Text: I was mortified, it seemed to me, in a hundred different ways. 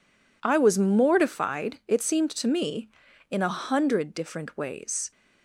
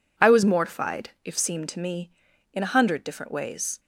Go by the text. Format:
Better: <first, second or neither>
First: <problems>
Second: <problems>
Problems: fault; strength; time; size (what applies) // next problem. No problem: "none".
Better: first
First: none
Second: says "if" for "it"; at 1.2 s